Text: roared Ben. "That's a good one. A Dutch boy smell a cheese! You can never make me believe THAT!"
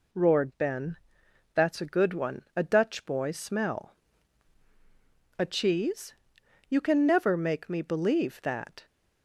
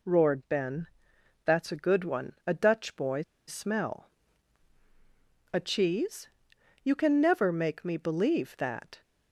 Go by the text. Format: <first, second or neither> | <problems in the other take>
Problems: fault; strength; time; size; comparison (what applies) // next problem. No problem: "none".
first | pauses between "boy" and "smell"; slight; at 3.2 s; 0.25 s long // pauses between "smell" and "a"; strong; at 4.0 s; 1.4 s long; strong in the first